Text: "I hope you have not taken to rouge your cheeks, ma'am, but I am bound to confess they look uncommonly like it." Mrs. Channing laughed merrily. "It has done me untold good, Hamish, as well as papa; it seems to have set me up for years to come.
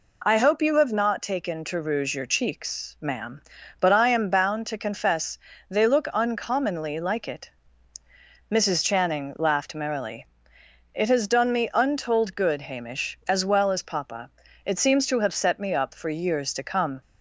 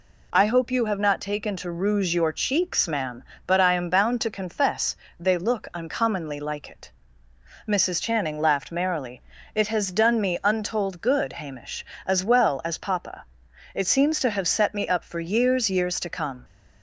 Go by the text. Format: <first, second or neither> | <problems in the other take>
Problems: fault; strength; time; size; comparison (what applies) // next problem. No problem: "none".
first | pauses between "confess" and "they"; slight; at 4.9 s; 0.24 s long; slight in the first // says "years" twice; at 15.7 s